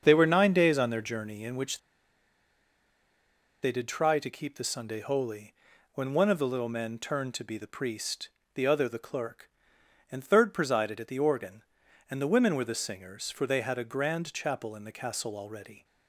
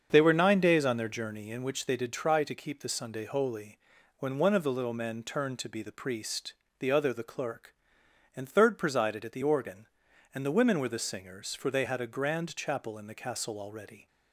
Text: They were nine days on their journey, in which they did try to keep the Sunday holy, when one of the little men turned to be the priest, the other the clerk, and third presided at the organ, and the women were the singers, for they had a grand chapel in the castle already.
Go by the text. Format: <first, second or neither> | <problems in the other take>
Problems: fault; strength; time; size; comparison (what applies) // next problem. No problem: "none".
second | starts louder than the rest; until 1.0 s; 7 dB; also in the second // pauses between "which" and "they"; strong; at 1.7 s; 1.8 s long